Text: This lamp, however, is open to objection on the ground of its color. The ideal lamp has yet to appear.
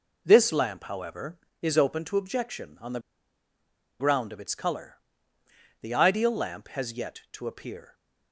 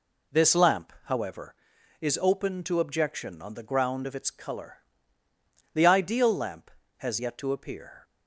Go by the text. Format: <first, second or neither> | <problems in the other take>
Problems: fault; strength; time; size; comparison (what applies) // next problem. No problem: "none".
second | pauses between "the" and "ground"; at 3.0 s; 0.99 s long